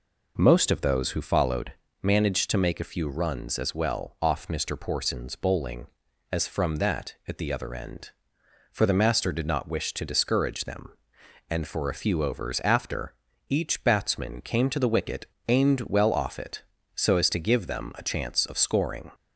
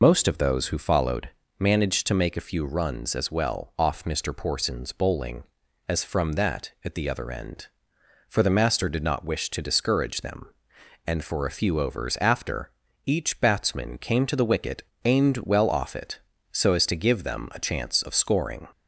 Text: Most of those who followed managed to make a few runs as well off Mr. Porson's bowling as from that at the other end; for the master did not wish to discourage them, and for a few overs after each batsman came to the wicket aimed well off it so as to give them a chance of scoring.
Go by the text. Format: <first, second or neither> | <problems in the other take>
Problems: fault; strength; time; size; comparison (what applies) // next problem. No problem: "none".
first | loses the start of "Most"; at 0.0 s; 95 ms // pauses between "followed" and "managed"; slight; at 1.2 s; 0.30 s long; slight in the first // pauses between "after" and "each"; slight; at 12.7 s; 0.34 s long; slight in the first // pauses between "wicket" and "aimed"; slight; at 14.8 s; 0.24 s long; slight in the first